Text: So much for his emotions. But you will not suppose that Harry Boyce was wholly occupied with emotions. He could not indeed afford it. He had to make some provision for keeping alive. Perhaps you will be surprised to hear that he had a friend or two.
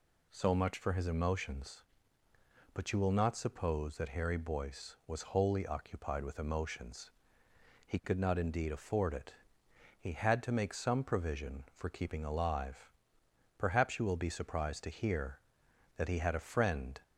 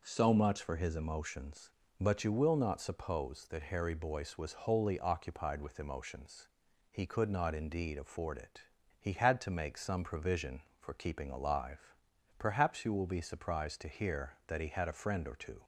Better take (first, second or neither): second